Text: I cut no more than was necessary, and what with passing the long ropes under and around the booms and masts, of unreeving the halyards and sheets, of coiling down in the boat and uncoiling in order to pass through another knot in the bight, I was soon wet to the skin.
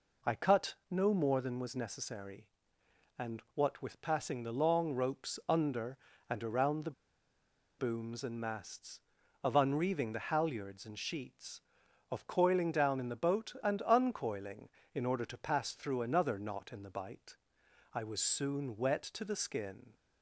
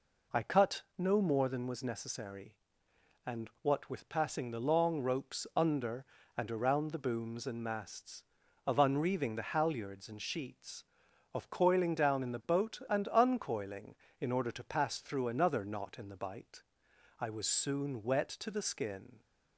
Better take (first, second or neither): second